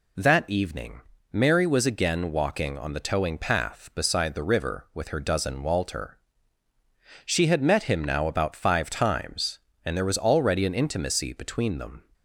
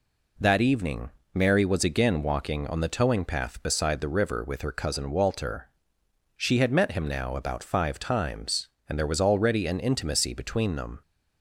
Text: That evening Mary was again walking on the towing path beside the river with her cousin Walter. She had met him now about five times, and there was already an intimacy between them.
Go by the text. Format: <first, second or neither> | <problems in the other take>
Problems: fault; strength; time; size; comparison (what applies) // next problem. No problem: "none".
second | pauses between "evening" and "Mary"; slight; at 1.0 s; 0.30 s long; slight in the second // says "dozen" for "cousin"; at 5.2 s